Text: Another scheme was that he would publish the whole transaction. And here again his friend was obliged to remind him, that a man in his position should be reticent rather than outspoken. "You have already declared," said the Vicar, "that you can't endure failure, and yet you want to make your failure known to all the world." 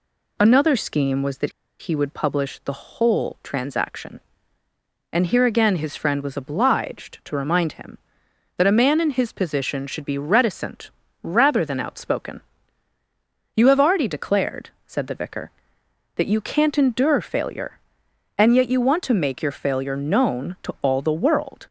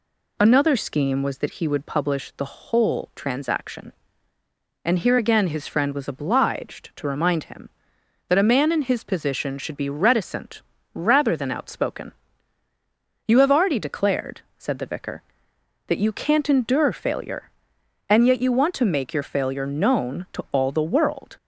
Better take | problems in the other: second | pauses between "that" and "he"; slight; at 1.5 s; 0.30 s long // pauses between "reticent" and "rather"; slight; at 10.9 s; 0.32 s long; slight in the second

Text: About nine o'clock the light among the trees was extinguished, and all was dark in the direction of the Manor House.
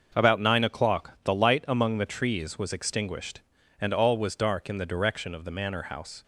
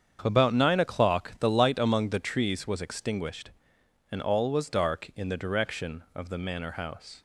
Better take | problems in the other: neither | starts louder than the rest; the same in both

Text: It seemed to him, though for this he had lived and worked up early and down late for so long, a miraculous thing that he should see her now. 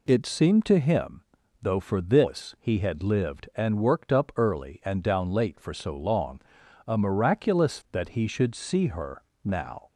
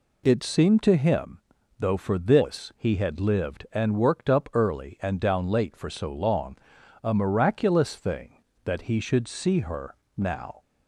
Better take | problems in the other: second | skips "thing"; at 7.8 s // pauses between "her" and "now"; slight; at 9.2 s; 0.20 s long; slight in the second

